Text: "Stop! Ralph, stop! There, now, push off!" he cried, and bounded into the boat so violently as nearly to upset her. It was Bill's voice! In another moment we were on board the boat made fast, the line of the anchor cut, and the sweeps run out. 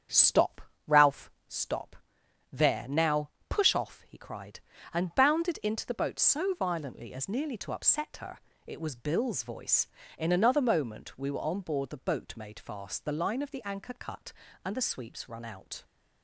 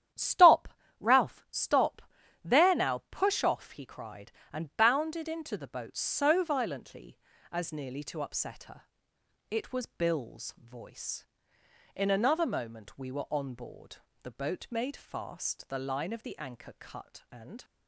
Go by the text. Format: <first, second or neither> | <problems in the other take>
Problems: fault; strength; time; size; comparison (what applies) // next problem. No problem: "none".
first | starts louder than the rest; strong; until 1.5 s; 10 dB; strong in the first // pauses between "board" and "the"; slight; at 13.9 s; 0.26 s long // stops before "the sweeps run out"; at 17.6 s